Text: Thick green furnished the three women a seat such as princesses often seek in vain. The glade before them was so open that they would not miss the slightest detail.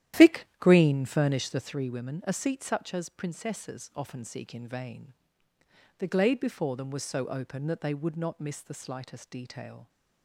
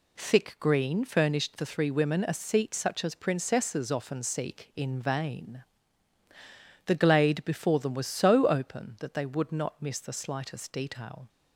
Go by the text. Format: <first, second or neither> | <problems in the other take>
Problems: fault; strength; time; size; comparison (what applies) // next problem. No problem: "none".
second | starts louder than the rest; strong; until 1.9 s; 12 dB